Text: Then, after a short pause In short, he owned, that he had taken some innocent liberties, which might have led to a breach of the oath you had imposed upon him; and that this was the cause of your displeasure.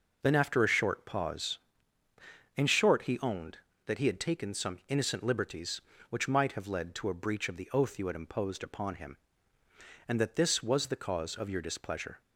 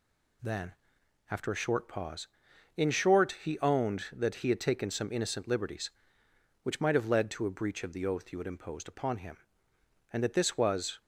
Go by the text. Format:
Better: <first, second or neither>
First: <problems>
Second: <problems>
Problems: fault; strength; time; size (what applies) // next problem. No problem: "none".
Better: first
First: none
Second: stops before "the cause of your displeasure"; at 11.0 s